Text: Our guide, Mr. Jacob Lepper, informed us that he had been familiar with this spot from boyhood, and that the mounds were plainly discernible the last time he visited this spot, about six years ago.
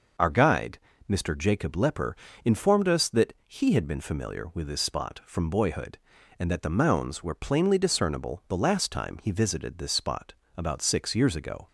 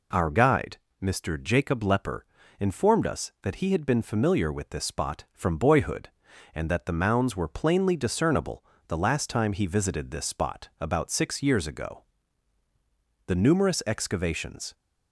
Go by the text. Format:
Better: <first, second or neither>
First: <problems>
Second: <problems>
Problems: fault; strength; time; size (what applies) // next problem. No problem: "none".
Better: first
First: none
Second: pauses between "discernible" and "the"; slight; at 8.6 s; 0.26 s long // goes on to say "The numerous excavations"; from 13.2 s on; 1.4 s long